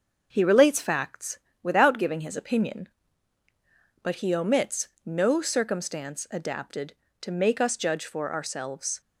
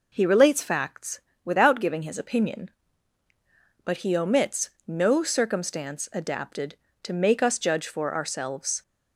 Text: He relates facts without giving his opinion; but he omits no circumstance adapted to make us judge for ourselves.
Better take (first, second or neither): second